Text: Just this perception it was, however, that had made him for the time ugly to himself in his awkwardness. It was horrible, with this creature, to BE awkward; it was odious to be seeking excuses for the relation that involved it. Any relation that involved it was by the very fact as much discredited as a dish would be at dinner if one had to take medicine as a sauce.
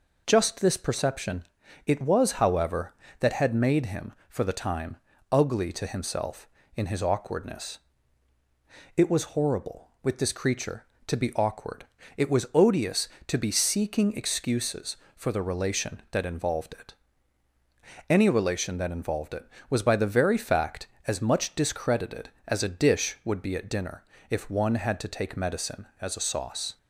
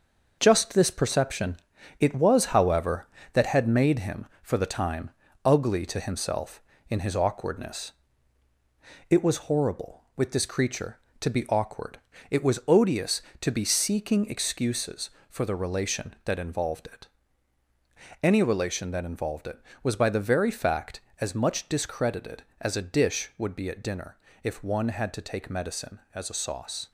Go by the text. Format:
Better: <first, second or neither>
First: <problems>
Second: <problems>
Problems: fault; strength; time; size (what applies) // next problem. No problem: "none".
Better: first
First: pauses between "perception" and "it"; at 1.4 s; 0.42 s long // pauses between "time" and "ugly"; slight; at 4.9 s; 0.34 s long // pauses between "dinner" and "if"; slight; at 24.0 s; 0.28 s long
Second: gets quieter; throughout; 6.5 dB // pauses between "perception" and "it"; at 1.5 s; 0.42 s long // pauses between "time" and "ugly"; slight; at 5.1 s; 0.34 s long // pauses between "dinner" and "if"; slight; at 24.1 s; 0.28 s long